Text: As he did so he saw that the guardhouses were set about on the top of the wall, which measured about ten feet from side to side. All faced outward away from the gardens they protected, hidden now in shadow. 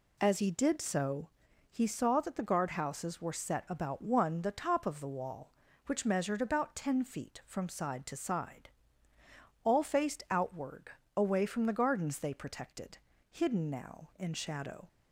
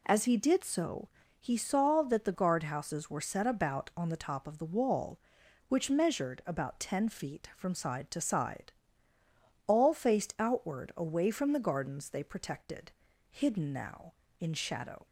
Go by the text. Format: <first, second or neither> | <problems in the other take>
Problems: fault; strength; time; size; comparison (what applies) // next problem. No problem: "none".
second | pauses between "so" and "he"; at 1.2 s; 0.40 s long; slight in the second // says "one" for "on"; at 4.0 s // pauses between "outward" and "away"; slight; at 10.8 s; 0.26 s long